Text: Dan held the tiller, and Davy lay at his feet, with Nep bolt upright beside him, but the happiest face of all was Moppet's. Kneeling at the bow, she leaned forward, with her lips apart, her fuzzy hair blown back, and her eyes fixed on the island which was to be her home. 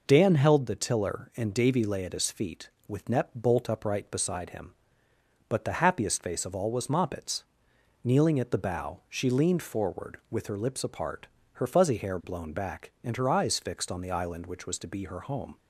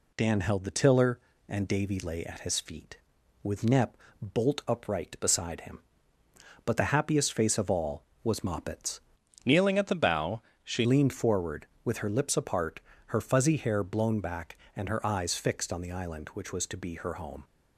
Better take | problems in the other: first | pauses between "Nep" and "bolt"; slight; at 3.9 s; 0.24 s long // changes voice from "Kneeling" to "she"; from 9.4 to 10.8 s; 1.4 s long

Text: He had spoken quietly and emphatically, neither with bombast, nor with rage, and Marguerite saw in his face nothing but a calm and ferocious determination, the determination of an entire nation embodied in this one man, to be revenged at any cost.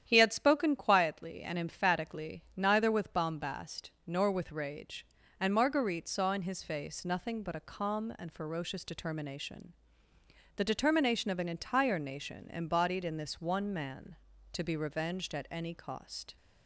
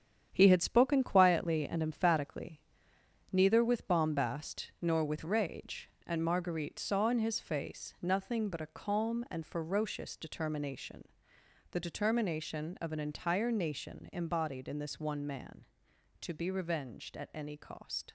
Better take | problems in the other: first | gets quieter; strong; throughout; 7.5 dB // starts louder than the rest; strong; until 1.3 s; 9 dB; strong in the first

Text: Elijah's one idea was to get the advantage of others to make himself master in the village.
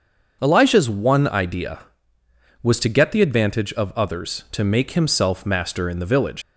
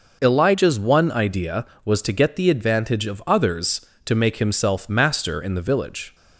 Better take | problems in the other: second | starts louder than the rest; until 1.4 s; 6.5 dB // leaves "village" unfinished; at 6.4 s; 100 ms

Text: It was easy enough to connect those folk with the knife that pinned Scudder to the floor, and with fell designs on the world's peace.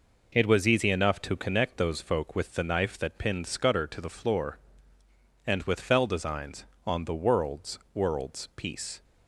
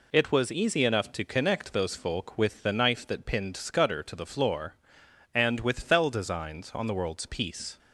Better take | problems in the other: second | says "world's" twice; at 7.9 s

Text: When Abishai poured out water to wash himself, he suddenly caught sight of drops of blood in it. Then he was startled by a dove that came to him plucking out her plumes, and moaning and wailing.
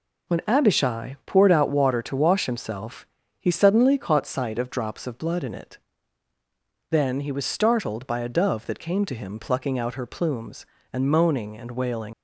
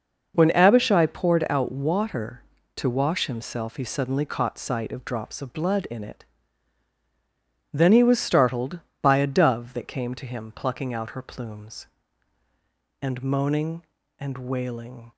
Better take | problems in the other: second | leaves "wailing" unfinished; at 12.1 s; 110 ms

